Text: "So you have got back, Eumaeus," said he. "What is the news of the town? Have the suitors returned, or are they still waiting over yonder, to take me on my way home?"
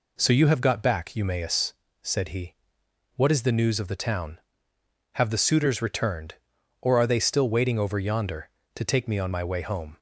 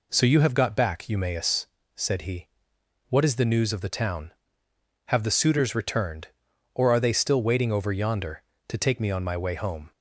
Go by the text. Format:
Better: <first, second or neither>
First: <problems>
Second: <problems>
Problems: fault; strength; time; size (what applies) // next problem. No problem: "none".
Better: neither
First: none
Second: none